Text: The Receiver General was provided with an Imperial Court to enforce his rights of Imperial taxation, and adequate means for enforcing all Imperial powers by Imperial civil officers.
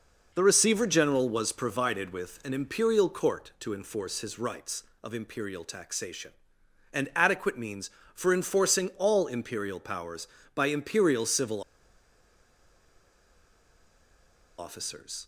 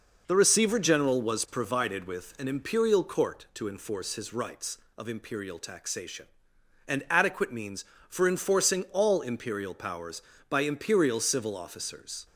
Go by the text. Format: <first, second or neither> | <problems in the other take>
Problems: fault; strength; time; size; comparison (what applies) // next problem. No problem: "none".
second | pauses between "civil" and "officers"; strong; at 11.6 s; 2.9 s long